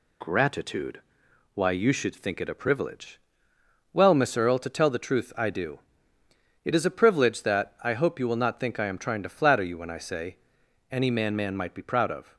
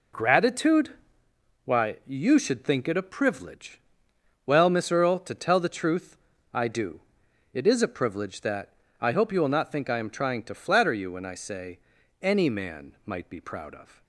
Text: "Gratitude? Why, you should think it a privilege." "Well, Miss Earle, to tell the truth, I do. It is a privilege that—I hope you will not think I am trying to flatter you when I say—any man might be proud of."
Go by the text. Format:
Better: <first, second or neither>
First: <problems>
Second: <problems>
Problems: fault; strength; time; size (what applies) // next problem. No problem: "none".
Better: second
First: says "man" twice; at 11.3 s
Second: none